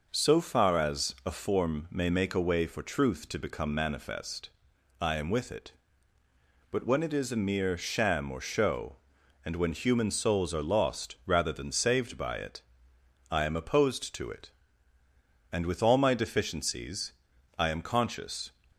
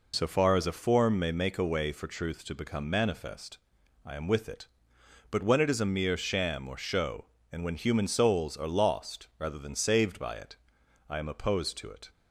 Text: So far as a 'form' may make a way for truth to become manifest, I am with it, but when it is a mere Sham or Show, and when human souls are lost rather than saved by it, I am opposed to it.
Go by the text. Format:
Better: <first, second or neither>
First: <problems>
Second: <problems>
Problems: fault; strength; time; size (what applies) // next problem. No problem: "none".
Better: second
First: goes on to say "And with all my deficiencies I am conscious"; strong; from 15.5 s on; 2.9 s long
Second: none